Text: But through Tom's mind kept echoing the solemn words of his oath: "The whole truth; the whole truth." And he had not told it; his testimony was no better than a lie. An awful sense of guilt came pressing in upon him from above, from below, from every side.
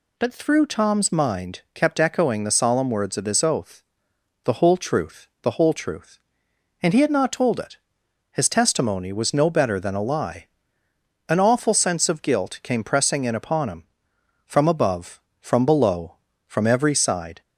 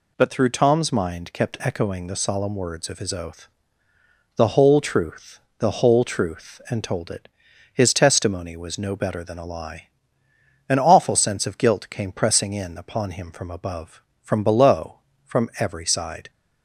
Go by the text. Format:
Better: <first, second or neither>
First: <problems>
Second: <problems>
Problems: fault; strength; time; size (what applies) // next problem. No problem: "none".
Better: first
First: none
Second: skips "he had not"; at 6.8 s